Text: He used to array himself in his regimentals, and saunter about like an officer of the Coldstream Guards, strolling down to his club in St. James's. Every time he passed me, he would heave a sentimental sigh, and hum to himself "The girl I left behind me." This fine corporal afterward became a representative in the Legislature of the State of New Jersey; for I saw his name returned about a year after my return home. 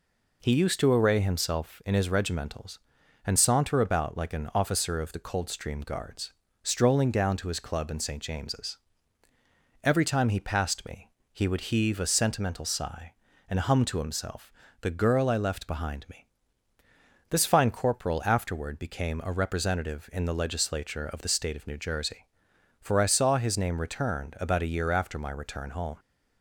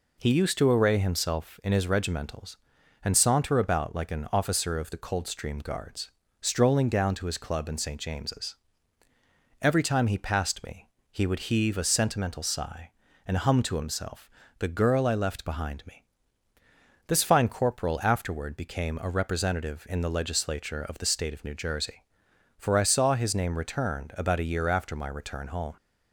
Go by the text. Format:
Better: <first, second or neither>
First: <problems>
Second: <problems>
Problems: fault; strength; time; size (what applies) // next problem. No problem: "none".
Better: neither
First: pauses between "himself" and "The"; slight; at 14.5 s; 0.30 s long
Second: pauses between "himself" and "The"; slight; at 14.2 s; 0.30 s long